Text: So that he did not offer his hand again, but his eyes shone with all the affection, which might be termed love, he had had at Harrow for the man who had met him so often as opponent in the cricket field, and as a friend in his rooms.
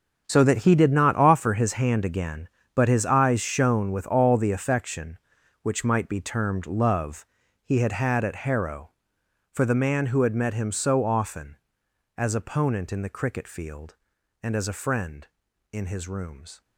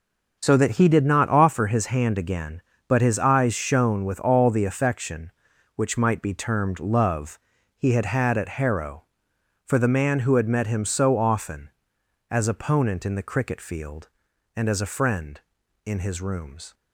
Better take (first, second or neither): second